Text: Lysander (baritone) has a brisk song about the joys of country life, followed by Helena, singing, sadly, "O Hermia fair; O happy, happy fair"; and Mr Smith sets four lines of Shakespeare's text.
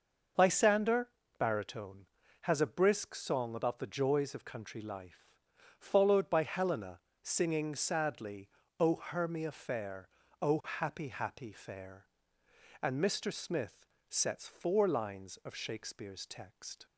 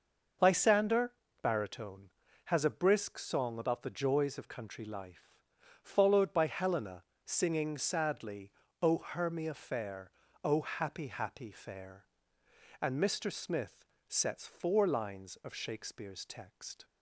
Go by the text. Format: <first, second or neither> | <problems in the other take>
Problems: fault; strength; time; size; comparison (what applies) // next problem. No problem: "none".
neither | starts louder than the rest; noticeable; the same in both // pauses between "Smith" and "sets"; slight; the same in both